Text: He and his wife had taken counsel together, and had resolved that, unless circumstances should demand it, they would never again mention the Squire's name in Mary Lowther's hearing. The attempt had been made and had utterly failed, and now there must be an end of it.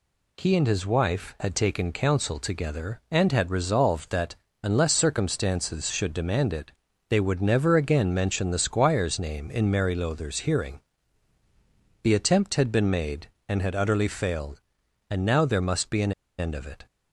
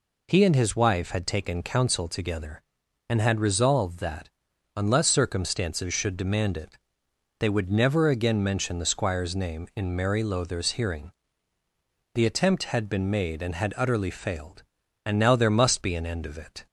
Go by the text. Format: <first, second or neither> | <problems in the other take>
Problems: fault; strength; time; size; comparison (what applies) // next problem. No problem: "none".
second | pauses between "an" and "end"; slight; at 16.1 s; 0.25 s long